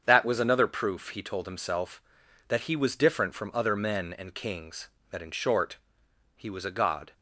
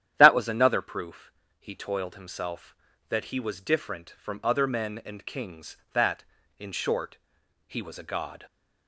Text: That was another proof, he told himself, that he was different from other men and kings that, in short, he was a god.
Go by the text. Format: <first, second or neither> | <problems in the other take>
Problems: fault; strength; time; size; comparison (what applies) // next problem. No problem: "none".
first | starts louder than the rest; strong; until 1.1 s; 10.5 dB; strong in the first // says "toiled" for "told"; at 1.7 s